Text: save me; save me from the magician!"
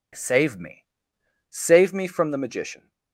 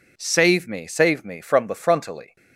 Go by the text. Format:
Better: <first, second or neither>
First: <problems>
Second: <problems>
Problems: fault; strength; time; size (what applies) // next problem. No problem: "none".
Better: first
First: none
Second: says "frontally" for "magician"; at 1.7 s